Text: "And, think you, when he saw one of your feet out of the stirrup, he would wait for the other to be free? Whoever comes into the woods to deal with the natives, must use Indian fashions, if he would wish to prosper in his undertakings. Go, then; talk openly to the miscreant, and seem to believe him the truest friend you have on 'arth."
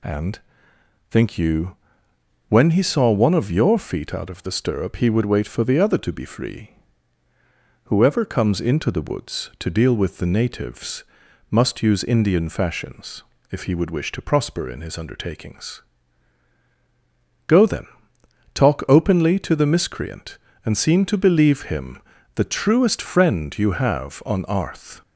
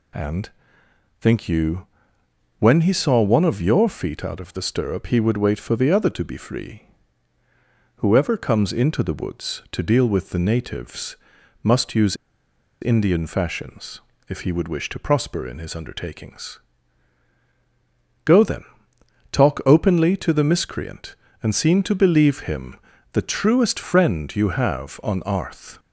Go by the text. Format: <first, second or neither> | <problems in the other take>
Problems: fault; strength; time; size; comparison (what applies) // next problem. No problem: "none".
first | pauses between "use" and "Indian"; noticeable; at 12.1 s; 0.67 s long // pauses between "him" and "the"; at 22.7 s; 0.38 s long; also in the first